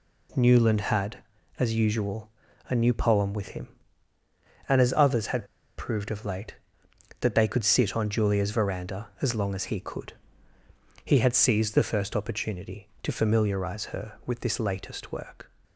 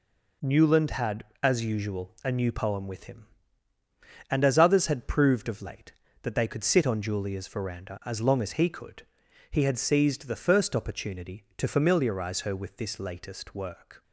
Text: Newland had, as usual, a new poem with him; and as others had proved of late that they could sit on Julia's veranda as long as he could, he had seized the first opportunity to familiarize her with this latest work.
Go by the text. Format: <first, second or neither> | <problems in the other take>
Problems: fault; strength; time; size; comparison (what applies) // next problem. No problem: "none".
second | pauses between "had" and "proved"; slight; at 5.4 s; 0.31 s long